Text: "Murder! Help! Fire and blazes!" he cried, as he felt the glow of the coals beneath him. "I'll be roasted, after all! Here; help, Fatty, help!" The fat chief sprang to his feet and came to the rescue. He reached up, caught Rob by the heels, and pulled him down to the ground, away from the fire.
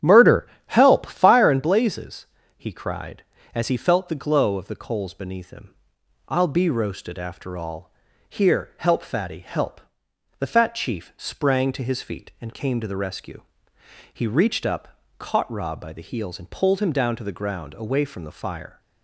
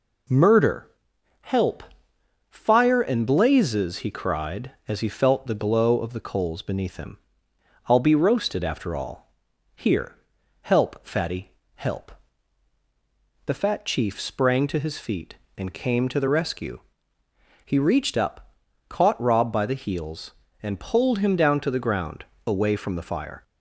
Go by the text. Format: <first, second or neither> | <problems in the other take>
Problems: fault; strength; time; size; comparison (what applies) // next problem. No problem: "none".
second | starts louder than the rest; strong; until 1.4 s; 10 dB